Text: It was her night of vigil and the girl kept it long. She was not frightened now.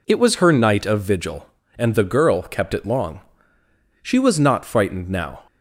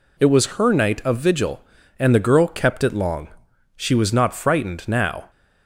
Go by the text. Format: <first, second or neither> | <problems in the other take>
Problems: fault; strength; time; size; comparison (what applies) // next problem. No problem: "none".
neither | none